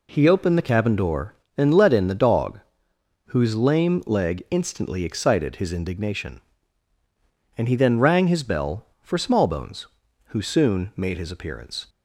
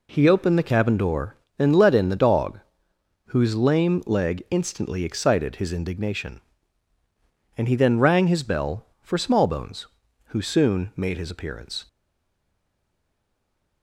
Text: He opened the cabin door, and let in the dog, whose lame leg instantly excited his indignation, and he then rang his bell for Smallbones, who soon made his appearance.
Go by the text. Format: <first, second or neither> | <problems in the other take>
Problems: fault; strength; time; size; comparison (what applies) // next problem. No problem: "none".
first | stays silent after the last word; noticeable; from 11.8 s on; 2.0 s long